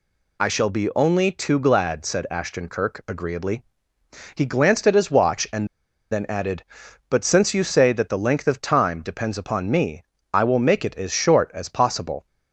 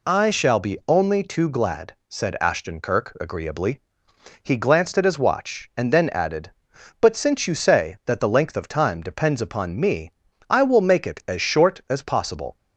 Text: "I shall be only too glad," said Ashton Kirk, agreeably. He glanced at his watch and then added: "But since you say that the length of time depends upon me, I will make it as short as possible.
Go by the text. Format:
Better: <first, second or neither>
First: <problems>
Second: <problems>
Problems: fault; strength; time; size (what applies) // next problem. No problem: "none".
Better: second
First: pauses between "and" and "then"; at 5.6 s; 0.44 s long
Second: none